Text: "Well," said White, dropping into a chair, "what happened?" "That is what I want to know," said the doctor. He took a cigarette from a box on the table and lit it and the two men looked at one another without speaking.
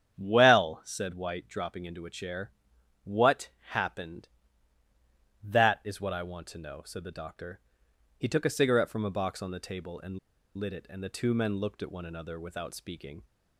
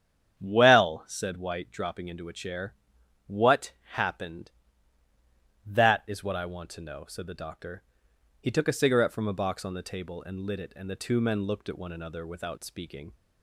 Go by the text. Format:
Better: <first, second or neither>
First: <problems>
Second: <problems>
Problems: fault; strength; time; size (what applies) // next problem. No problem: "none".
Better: second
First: starts louder than the rest; strong; until 1.2 s; 9 dB // pauses between "what" and "happened"; slight; at 3.4 s; 0.20 s long // pauses between "and" and "lit"; at 10.1 s; 0.39 s long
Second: starts louder than the rest; strong; until 1.4 s; 9 dB // pauses between "what" and "happened"; slight; at 3.7 s; 0.20 s long